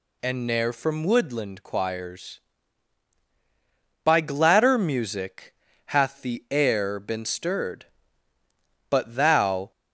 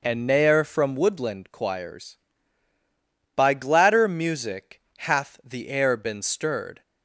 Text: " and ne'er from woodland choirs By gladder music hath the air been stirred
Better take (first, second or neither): second